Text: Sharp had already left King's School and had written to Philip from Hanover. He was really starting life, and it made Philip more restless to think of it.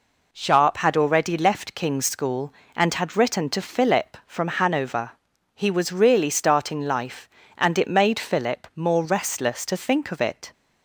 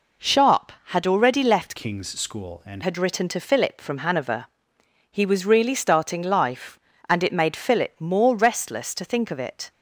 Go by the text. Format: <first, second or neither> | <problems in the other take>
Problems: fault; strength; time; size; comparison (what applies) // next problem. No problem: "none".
first | changes voice from "King's" to "and"; from 1.7 to 2.8 s; 1.1 s long